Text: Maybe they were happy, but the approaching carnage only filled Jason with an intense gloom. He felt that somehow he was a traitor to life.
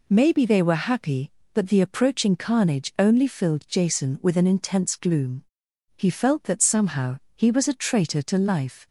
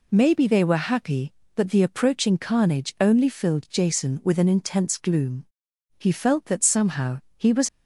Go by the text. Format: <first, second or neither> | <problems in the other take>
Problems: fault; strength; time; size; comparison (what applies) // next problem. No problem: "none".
first | pauses between "somehow" and "he"; slight; at 7.1 s; 0.18 s long; slight in the first // stops before "a traitor to life"; at 7.6 s